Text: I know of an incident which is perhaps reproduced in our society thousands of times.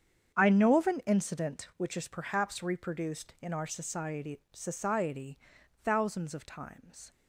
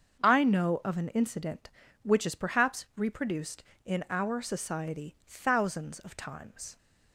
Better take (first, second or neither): second